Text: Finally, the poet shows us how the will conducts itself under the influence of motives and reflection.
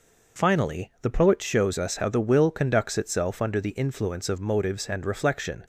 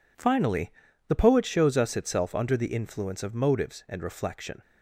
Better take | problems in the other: first | skips "how the will conducts"; at 1.9 s

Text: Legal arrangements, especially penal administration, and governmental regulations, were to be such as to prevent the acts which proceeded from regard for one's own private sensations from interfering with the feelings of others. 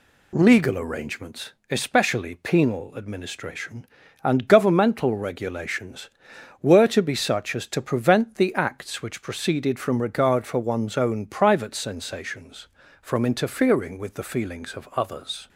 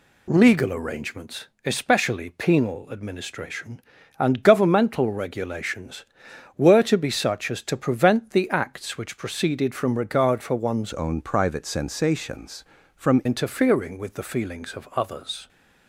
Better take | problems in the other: first | changes voice from "own" to "from"; from 10.9 to 13.2 s; 2.3 s long

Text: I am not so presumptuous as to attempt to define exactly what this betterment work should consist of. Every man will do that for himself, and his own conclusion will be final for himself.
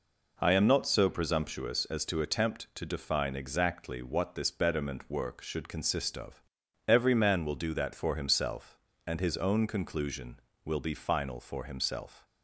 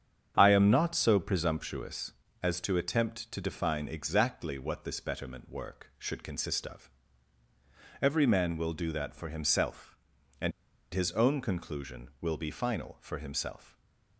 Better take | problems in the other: first | starts louder than the rest; strong; until 1.3 s; 8 dB // pauses between "and" and "his"; at 10.5 s; 0.42 s long // stays silent after the last word; slight; from 13.6 s on; 0.5 s long

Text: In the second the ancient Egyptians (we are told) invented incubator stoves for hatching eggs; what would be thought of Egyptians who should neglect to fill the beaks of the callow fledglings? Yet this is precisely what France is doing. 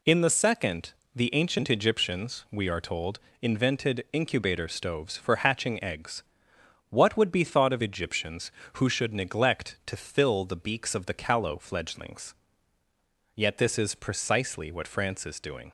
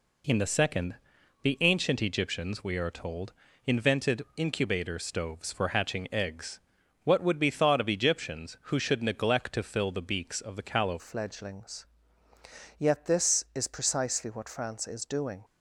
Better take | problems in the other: first | pauses between "second" and "the"; noticeable; at 0.9 s; 0.48 s long; slight in the first // changes voice at "fledglings"; from 10.9 s on; 4.5 s long

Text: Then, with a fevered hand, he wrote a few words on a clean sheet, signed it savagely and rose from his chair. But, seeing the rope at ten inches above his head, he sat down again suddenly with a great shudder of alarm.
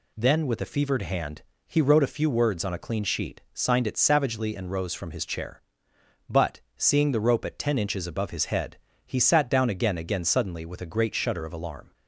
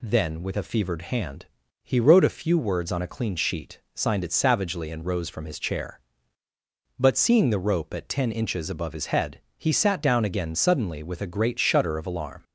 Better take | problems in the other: second | says "again" twice; at 9.9 s

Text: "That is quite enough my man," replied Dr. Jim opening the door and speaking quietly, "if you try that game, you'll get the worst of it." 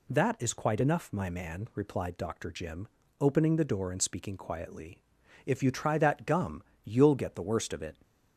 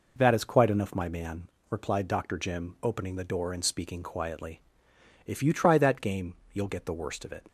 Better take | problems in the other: second | pauses between "Jim" and "opening"; slight; at 2.8 s; 0.32 s long // says "gum" for "game"; at 6.2 s

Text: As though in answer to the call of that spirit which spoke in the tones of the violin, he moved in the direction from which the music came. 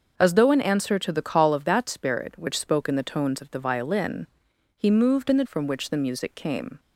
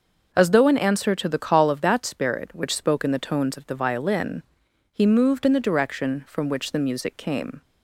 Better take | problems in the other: second | starts louder than the rest; until 1.1 s; 6.5 dB; noticeable in the second // skips "direction"; at 5.4 s

